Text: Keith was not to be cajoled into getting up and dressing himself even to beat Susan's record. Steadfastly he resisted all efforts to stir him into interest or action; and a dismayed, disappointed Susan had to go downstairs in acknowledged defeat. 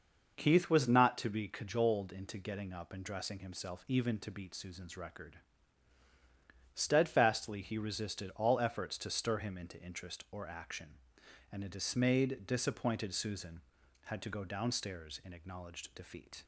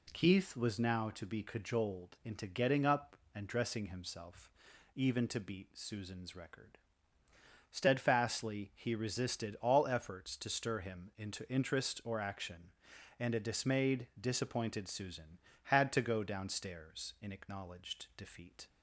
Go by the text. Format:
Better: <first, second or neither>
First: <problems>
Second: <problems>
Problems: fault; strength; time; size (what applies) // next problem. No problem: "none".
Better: first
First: none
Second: says "now" for "not"; at 0.7 s // pauses between "himself" and "even"; at 4.5 s; 0.44 s long